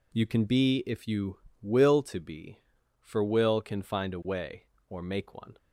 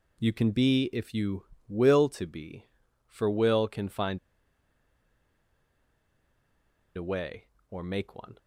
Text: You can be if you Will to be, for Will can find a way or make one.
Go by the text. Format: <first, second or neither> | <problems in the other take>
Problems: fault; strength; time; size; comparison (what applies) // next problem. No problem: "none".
first | pauses between "find" and "a"; strong; at 4.1 s; 2.7 s long